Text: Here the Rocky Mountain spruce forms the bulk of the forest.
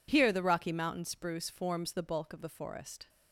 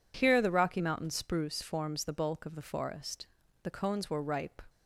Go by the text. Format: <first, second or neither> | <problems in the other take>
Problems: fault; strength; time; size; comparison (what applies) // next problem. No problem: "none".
first | goes on to say "The cones were ripe"; noticeable; from 3.6 s on; 0.96 s long